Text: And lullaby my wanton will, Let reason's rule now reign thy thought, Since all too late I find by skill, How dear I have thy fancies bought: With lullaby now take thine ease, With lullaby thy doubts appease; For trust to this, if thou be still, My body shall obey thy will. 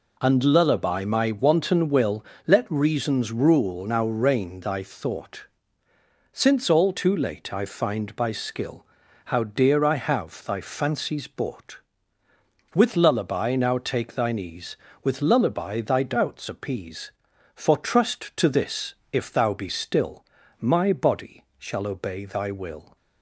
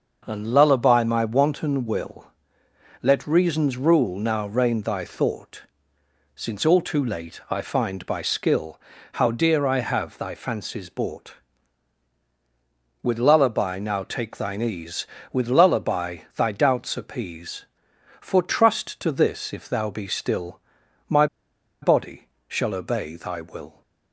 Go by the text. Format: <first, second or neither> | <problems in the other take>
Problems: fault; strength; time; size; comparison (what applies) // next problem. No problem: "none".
first | starts louder than the rest; noticeable; until 1.2 s; 6 dB // pauses between "lullaby" and "thy"; slight; at 16.1 s; 0.18 s long // pauses between "My" and "body"; noticeable; at 21.2 s; 0.56 s long // pauses between "body" and "shall"; slight; at 22.2 s; 0.20 s long; slight in the first